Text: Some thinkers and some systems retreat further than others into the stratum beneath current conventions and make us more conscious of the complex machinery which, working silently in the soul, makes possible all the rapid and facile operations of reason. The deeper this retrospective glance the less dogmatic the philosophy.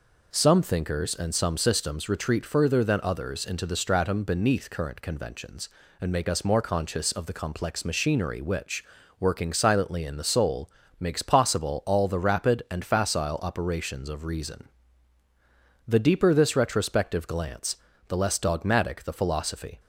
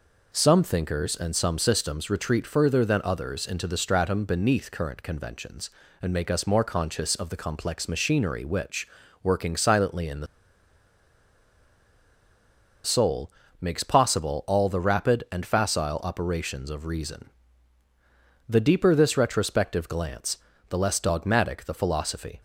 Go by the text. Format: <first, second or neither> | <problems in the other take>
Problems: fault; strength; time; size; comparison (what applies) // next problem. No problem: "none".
first | pauses between "the" and "soul"; strong; at 10.2 s; 2.5 s long // pauses between "glance" and "the"; slight; at 20.3 s; 0.32 s long; slight in the first